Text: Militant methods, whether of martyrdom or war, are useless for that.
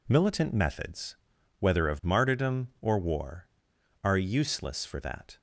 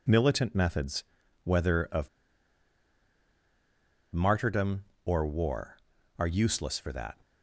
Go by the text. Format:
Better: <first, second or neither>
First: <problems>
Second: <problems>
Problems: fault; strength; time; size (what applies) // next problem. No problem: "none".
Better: first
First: none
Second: pauses between "of" and "martyrdom"; strong; at 2.0 s; 2.0 s long